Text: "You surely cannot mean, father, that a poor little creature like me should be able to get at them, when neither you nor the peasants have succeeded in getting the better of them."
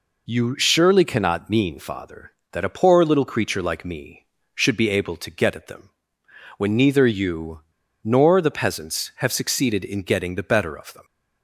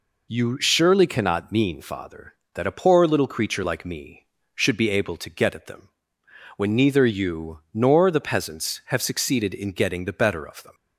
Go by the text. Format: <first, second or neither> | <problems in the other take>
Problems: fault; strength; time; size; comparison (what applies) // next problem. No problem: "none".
second | pauses between "you" and "nor"; at 7.6 s; 0.41 s long